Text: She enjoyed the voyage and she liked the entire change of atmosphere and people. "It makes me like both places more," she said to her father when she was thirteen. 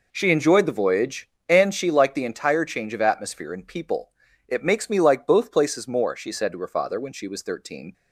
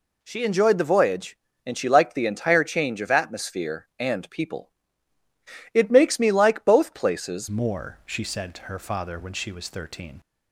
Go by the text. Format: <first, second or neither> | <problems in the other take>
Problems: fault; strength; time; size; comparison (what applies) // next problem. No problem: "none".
first | changes voice at "more"; from 7.4 s on; 2.7 s long